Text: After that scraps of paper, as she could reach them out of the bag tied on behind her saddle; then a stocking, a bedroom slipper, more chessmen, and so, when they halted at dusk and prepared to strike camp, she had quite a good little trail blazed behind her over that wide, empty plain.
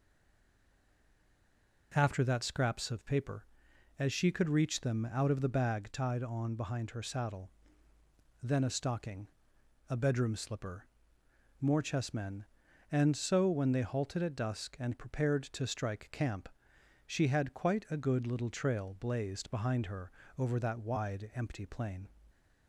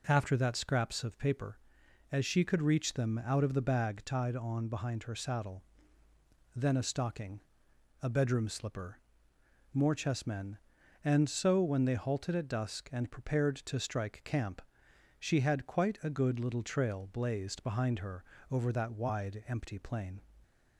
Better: second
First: stays silent before the first word; noticeable; until 1.9 s; 1.9 s long // pauses between "her" and "over"; slight; at 20.1 s; 0.28 s long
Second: pauses between "her" and "over"; slight; at 18.2 s; 0.28 s long

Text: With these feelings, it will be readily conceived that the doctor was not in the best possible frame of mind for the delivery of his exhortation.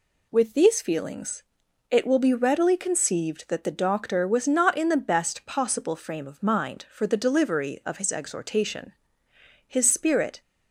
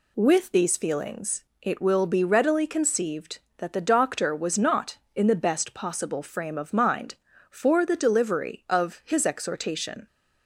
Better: second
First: goes on to say "His spirit"; noticeable; from 9.6 s on; 0.74 s long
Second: none

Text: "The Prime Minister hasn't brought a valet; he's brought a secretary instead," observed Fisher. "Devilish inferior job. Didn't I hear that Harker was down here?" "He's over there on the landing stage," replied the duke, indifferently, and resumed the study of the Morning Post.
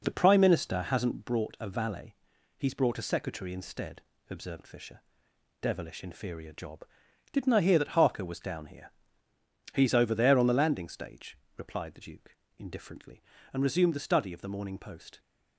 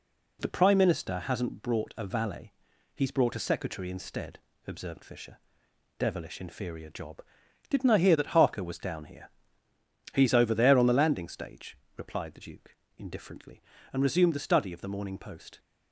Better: second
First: starts louder than the rest; noticeable; until 1.4 s; 4.5 dB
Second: none

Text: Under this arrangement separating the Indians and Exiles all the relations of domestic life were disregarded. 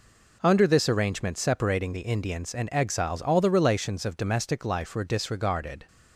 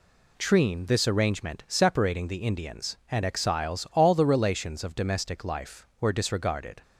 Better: first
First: none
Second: says "Treen" for "Under"; at 0.3 s

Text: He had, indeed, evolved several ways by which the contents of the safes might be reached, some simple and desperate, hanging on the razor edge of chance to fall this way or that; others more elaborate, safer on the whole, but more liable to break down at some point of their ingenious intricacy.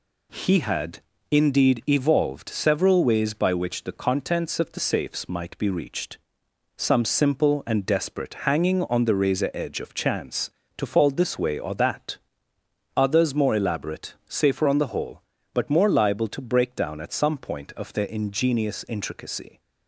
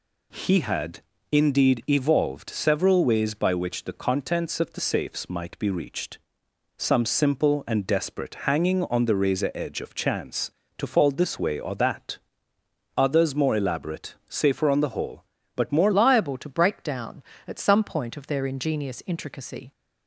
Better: first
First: none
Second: changes voice at "liable"; from 15.9 s on; 3.8 s long

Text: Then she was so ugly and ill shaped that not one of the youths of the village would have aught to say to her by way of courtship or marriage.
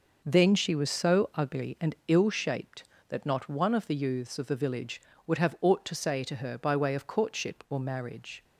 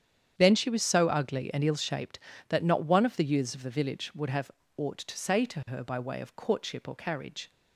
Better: first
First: none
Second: starts louder than the rest; strong; until 1.3 s; 8.5 dB // pauses between "have" and "aught"; slight; at 4.5 s; 0.26 s long // says "carriage" for "marriage"; at 6.9 s

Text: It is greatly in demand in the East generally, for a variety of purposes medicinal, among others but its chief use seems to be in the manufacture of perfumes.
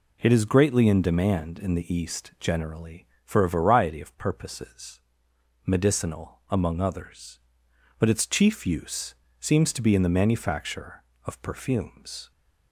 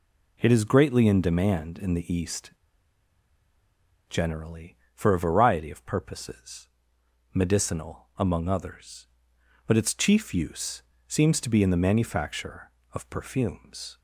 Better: first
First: pauses between "purposes" and "medicinal"; noticeable; at 4.9 s; 0.64 s long // pauses between "use" and "seems"; slight; at 9.1 s; 0.26 s long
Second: pauses between "East" and "generally"; strong; at 2.5 s; 1.5 s long // pauses between "purposes" and "medicinal"; noticeable; at 6.6 s; 0.64 s long // pauses between "use" and "seems"; slight; at 10.8 s; 0.26 s long

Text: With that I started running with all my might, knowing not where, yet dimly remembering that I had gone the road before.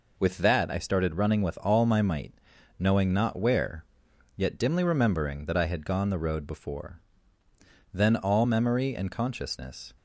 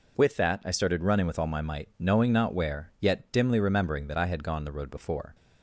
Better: second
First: goes on to say "Then all memory and consciousness"; strong; from 7.9 s on; 1.9 s long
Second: none

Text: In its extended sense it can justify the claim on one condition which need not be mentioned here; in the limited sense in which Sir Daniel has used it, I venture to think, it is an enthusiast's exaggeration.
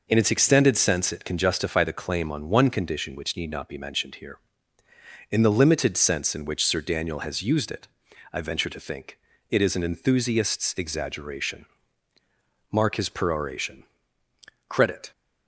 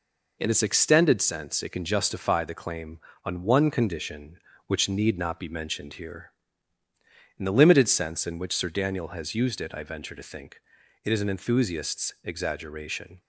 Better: second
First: goes on to say "Mark his peroration Credit"; strong; from 12.7 s on; 2.4 s long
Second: none

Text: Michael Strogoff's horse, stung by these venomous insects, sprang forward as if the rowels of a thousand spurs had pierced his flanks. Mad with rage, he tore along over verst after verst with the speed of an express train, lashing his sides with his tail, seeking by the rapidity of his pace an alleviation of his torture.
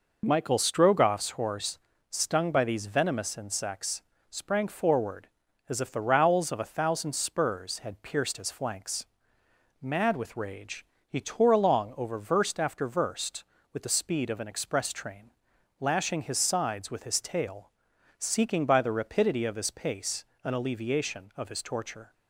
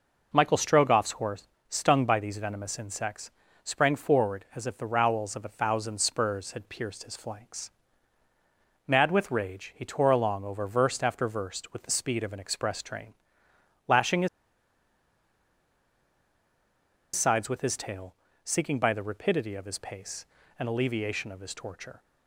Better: first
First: pauses between "pace" and "an"; slight; at 20.2 s; 0.20 s long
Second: pauses between "his" and "sides"; strong; at 14.2 s; 2.8 s long // pauses between "pace" and "an"; slight; at 20.2 s; 0.32 s long

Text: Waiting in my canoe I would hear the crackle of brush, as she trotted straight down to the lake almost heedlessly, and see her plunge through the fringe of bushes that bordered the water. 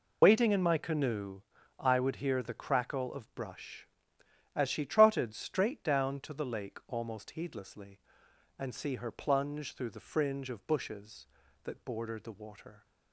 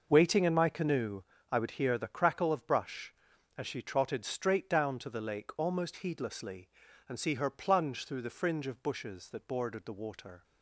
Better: second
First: loses the start of "Waiting"; at 0.2 s; 85 ms // pauses between "canoe" and "I"; at 1.3 s; 0.40 s long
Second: pauses between "canoe" and "I"; slight; at 1.2 s; 0.30 s long

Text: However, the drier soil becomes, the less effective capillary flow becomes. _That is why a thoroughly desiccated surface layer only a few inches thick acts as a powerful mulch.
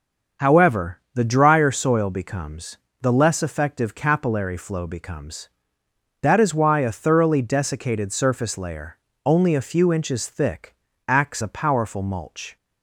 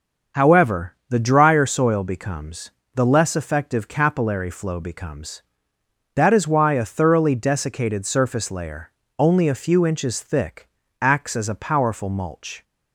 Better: second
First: starts louder than the rest; until 1.5 s; 6.5 dB // pauses between "layer" and "only"; slight; at 8.9 s; 0.28 s long // pauses between "thick" and "acts"; slight; at 10.7 s; 0.34 s long // skips "as"; at 11.4 s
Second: starts louder than the rest; until 1.4 s; 6.5 dB // pauses between "layer" and "only"; slight; at 8.9 s; 0.28 s long // pauses between "thick" and "acts"; slight; at 10.6 s; 0.34 s long

